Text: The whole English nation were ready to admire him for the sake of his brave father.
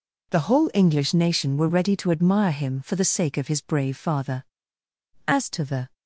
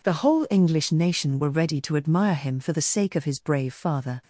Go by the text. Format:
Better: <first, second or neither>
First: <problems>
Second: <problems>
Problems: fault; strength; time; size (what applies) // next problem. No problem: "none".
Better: second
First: goes on to say "As to the"; noticeable; from 5.2 s on; 0.66 s long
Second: none